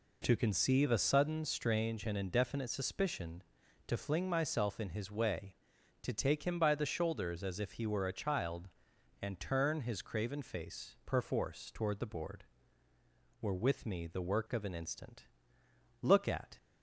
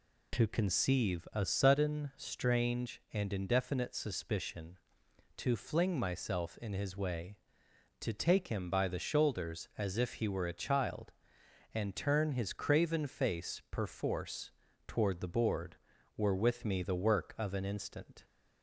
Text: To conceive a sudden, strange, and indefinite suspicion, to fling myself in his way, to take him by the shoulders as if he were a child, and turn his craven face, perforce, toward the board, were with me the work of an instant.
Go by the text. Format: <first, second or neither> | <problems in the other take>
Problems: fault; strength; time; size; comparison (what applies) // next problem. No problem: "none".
second | goes on to say "Look at"; from 16.0 s on; 0.56 s long